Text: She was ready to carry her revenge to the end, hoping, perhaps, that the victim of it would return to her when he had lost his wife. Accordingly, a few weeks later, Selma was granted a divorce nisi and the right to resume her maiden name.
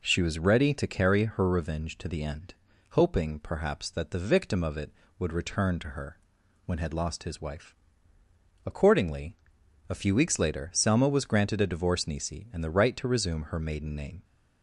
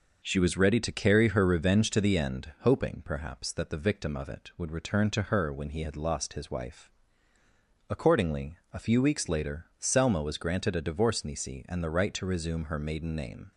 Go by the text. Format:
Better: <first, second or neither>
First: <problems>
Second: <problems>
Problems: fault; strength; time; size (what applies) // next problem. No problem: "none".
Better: second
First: pauses between "her" and "when"; noticeable; at 6.1 s; 0.48 s long // skips "he"; at 6.7 s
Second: none